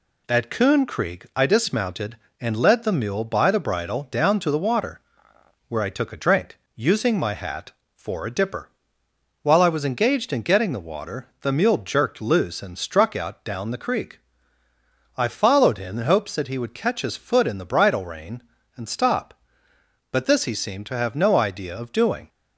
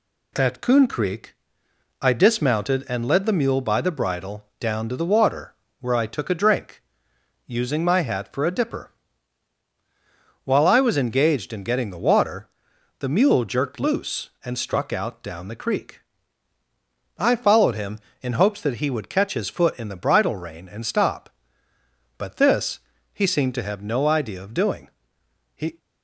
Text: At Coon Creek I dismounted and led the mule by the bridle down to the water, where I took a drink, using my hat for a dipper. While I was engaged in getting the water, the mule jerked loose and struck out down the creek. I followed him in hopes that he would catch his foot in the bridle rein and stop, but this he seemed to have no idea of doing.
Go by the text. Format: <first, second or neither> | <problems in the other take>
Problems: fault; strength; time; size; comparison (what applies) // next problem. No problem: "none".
first | pauses between "Creek" and "I"; noticeable; at 1.3 s; 0.68 s long // pauses between "this" and "he"; slight; at 22.7 s; 0.32 s long // goes on to say "He"; slight; from 25.5 s on; 0.24 s long